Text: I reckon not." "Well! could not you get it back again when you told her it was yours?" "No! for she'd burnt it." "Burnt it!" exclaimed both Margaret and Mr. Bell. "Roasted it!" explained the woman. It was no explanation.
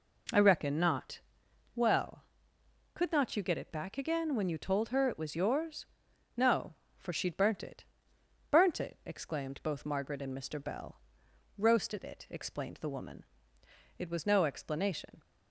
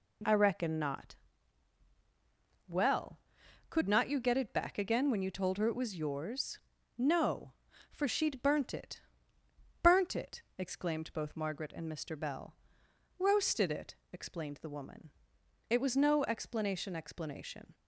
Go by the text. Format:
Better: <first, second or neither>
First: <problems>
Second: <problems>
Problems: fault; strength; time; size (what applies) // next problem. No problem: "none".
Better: first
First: none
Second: says "explanation" twice; at 16.9 s